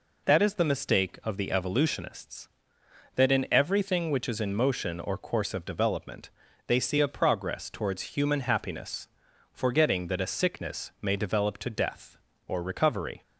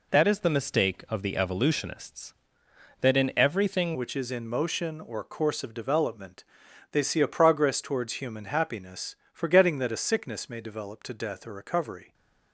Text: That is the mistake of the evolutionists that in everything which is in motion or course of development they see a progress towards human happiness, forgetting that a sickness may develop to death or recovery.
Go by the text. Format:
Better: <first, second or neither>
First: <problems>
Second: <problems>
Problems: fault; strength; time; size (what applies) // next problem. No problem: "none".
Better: first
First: pauses between "development" and "they"; at 6.2 s; 0.38 s long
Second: changes voice at "which"; from 3.9 s on; 8.2 s long // pauses between "development" and "they"; noticeable; at 6.4 s; 0.48 s long